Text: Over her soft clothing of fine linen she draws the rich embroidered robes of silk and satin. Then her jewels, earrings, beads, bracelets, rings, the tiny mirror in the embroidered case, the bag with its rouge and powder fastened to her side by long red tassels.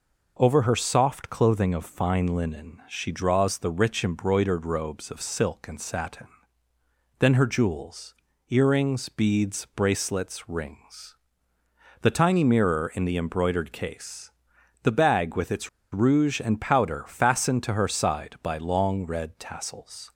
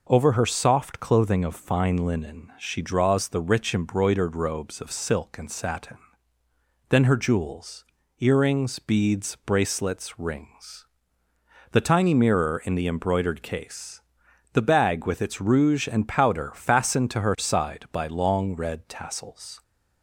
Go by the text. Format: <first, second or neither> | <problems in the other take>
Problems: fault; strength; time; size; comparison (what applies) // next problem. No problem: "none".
second | pauses between "its" and "rouge"; slight; at 15.6 s; 0.25 s long